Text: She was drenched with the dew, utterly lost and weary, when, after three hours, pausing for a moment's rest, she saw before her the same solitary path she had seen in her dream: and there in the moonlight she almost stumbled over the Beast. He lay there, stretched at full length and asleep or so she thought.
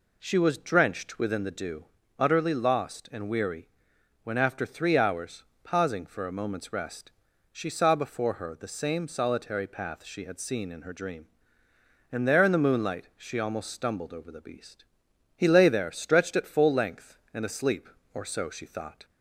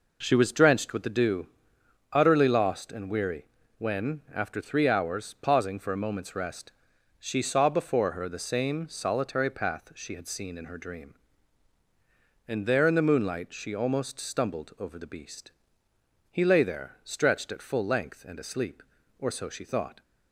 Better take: second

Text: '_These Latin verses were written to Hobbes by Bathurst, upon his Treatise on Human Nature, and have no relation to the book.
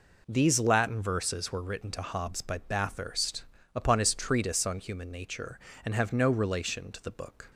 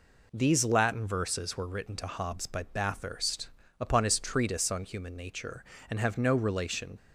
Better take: first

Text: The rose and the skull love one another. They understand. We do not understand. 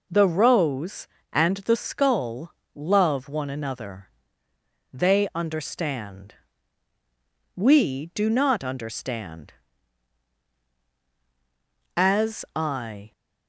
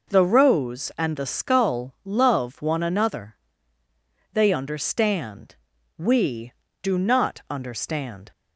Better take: second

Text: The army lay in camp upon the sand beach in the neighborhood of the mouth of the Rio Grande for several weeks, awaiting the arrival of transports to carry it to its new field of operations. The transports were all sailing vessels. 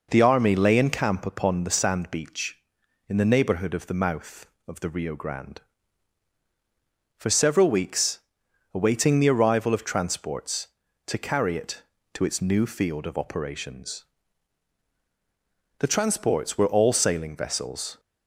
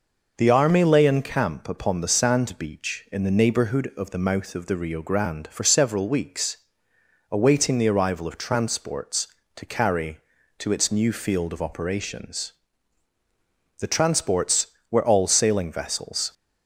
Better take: first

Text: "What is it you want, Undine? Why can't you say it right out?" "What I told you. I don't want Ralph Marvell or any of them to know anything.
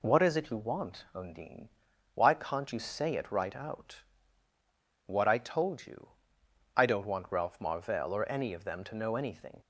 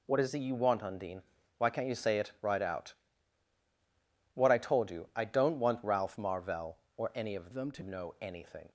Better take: first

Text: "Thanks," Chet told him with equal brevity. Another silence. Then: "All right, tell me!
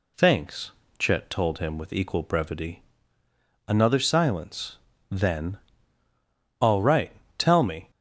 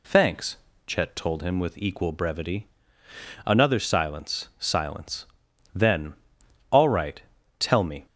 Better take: first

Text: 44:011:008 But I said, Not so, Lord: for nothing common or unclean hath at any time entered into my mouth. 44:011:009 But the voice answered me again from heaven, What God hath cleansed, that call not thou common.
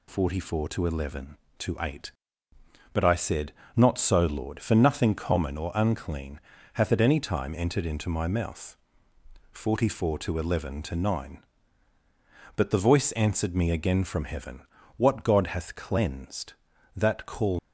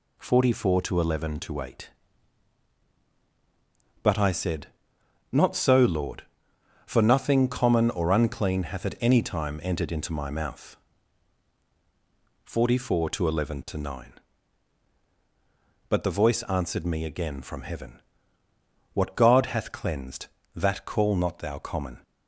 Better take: second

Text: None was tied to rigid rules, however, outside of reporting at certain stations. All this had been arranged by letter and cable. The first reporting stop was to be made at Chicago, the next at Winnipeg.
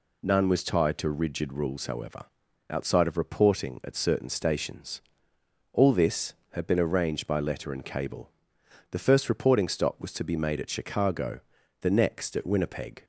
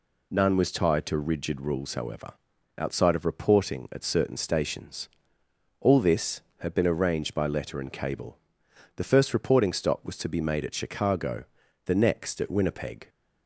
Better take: neither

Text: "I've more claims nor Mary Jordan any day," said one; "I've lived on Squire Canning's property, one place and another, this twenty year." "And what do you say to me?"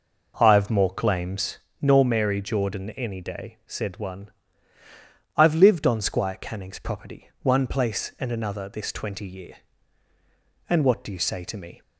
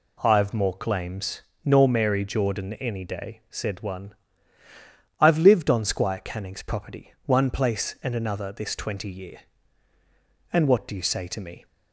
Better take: second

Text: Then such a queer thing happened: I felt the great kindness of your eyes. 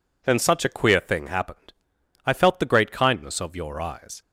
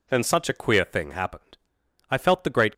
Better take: first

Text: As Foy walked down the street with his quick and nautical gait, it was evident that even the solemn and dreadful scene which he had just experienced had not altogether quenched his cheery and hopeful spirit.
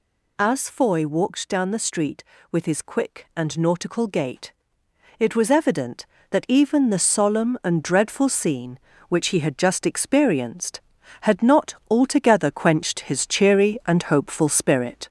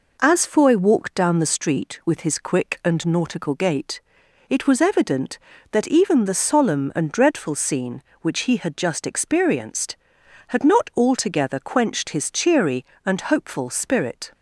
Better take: second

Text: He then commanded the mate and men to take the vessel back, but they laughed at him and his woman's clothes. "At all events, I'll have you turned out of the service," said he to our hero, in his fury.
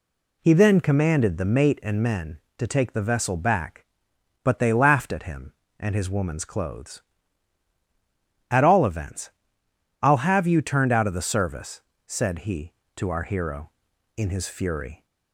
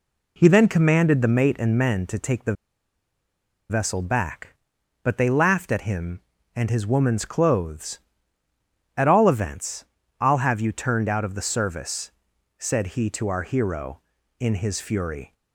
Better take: first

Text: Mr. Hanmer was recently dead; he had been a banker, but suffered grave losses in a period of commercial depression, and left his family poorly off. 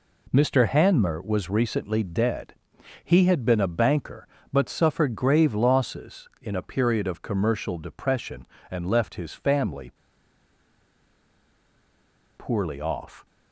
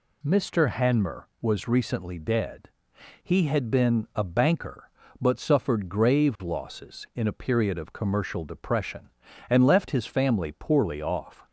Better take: second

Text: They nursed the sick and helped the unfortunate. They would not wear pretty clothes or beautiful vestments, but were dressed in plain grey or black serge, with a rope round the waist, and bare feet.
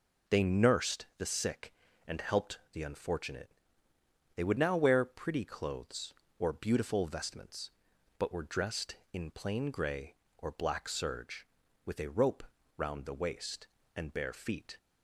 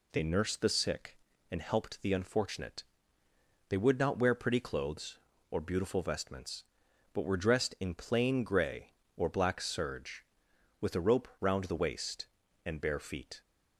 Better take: second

